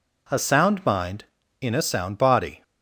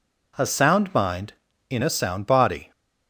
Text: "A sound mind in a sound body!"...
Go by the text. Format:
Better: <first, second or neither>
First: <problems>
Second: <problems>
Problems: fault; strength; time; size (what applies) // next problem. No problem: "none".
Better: neither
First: none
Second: none